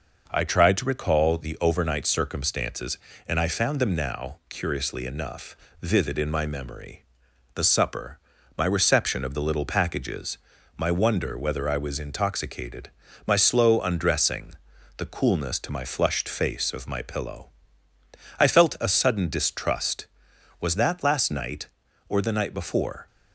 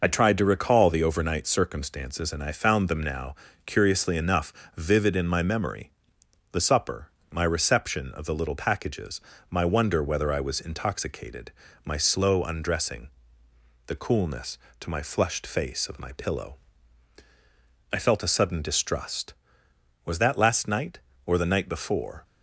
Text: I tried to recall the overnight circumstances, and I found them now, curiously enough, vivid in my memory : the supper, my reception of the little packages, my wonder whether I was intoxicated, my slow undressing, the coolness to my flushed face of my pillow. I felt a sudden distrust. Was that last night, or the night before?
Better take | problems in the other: first | loses the start of "I"; at 0.0 s; 40 ms

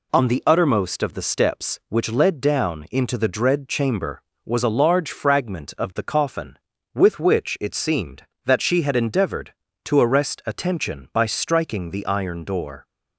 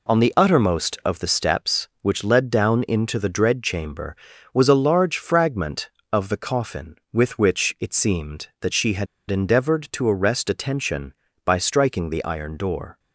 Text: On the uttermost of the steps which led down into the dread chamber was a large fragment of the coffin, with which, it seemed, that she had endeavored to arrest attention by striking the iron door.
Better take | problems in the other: first | pauses between "had" and "endeavored"; slight; at 9.0 s; 0.24 s long

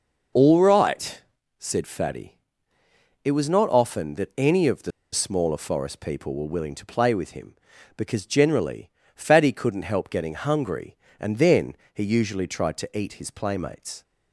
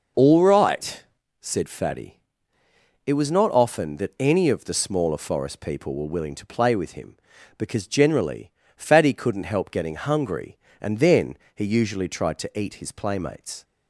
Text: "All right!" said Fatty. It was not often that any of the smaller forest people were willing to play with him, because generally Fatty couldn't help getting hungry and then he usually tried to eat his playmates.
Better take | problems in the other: second | pauses between "the" and "smaller"; slight; at 4.9 s; 0.21 s long // pauses between "generally" and "Fatty"; slight; at 8.9 s; 0.24 s long; slight in the second // pauses between "then" and "he"; slight; at 11.7 s; 0.16 s long; slight in the second

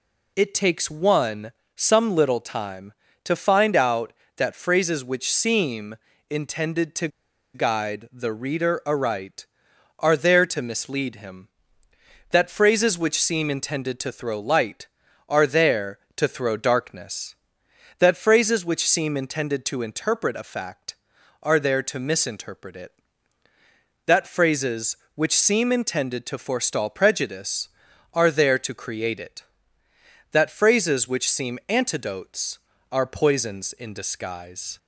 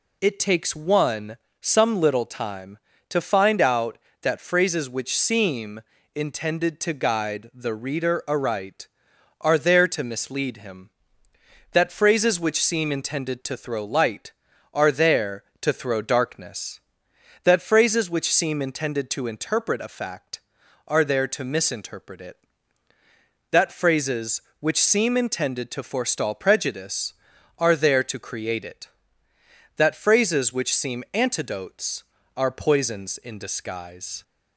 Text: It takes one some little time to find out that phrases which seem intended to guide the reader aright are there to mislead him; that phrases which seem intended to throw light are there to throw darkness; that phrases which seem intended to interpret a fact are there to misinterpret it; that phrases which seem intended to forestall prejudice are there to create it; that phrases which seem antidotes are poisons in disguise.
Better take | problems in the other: second | pauses between "one" and "some"; slight; at 1.5 s; 0.24 s long; slight in the second // pauses between "seem" and "intended"; slight; at 5.9 s; 0.32 s long; slight in the second // pauses between "to" and "guide"; noticeable; at 7.0 s; 0.46 s long

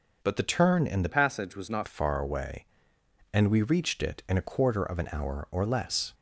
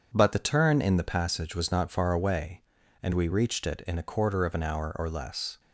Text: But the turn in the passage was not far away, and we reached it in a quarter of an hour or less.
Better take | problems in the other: second | changes voice from "passage" to "not"; from 1.0 to 1.8 s; 0.8 s long

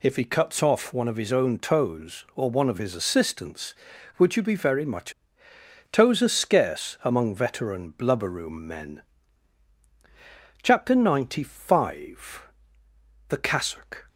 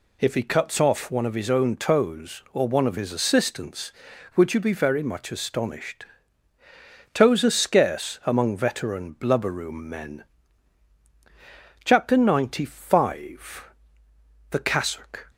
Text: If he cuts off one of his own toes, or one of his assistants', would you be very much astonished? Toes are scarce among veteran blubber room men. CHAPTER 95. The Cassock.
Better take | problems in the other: second | skips "astonished"; at 5.5 s

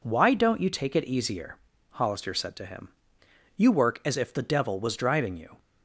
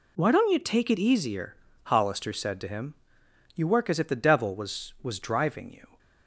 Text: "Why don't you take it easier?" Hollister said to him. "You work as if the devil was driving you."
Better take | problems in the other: first | says "was" twice; at 5.0 s

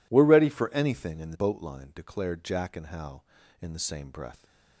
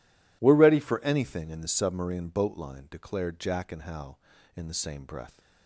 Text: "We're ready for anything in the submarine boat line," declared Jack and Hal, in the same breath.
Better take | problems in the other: second | skips "submarine"; at 1.3 s

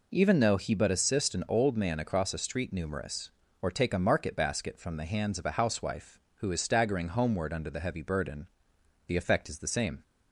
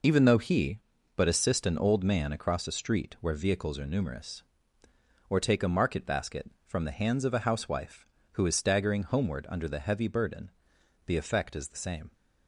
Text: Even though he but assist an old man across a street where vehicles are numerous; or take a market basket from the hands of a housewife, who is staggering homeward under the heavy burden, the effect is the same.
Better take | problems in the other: second | skips "where vehicles are"; at 2.7 s

